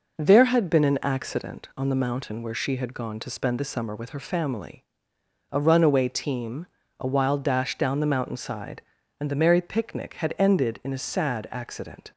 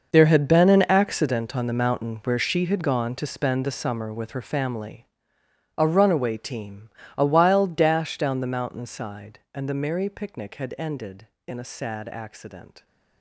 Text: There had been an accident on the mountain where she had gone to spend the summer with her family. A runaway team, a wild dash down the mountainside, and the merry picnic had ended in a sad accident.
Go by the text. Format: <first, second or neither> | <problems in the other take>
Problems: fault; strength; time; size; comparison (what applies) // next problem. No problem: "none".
first | gets quieter; strong; throughout; 15 dB